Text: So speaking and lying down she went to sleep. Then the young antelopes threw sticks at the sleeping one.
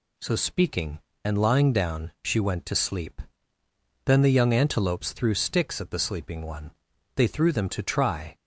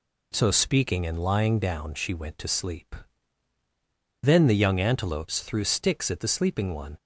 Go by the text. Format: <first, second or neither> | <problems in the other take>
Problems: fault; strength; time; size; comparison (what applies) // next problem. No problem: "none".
second | goes on to say "They threw them to try"; noticeable; from 7.1 s on; 1.1 s long